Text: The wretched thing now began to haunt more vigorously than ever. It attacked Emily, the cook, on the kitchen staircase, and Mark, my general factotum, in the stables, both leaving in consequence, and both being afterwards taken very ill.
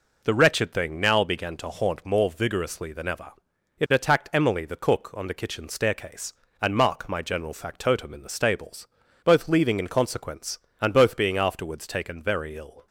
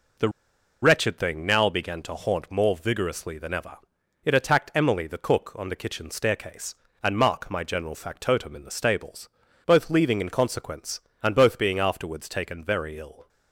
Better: first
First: none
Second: pauses between "The" and "wretched"; noticeable; at 0.2 s; 0.52 s long

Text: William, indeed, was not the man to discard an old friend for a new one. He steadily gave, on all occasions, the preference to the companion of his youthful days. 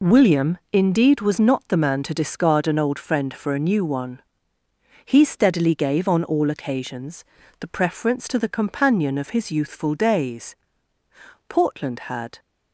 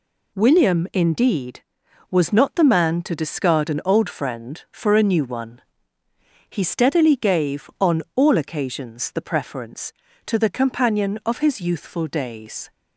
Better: second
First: goes on to say "Portland had"; noticeable; from 11.4 s on; 0.90 s long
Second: none

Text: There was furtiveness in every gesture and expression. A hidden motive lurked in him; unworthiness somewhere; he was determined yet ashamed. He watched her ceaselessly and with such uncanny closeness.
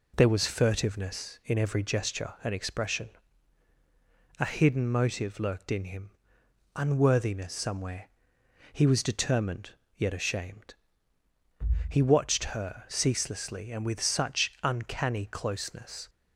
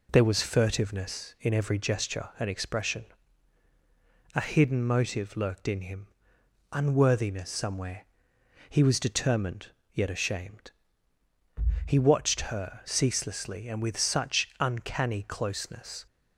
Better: neither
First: pauses between "determined" and "yet"; slight; at 9.7 s; 0.26 s long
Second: pauses between "determined" and "yet"; slight; at 9.6 s; 0.26 s long

